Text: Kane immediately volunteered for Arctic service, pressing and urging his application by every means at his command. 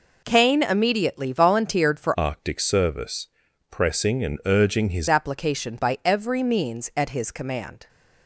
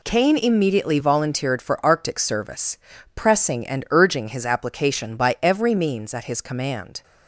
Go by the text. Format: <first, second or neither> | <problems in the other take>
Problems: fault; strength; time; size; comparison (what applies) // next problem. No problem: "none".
second | changes voice from "Arctic" to "his"; from 2.1 to 5.0 s; 2.9 s long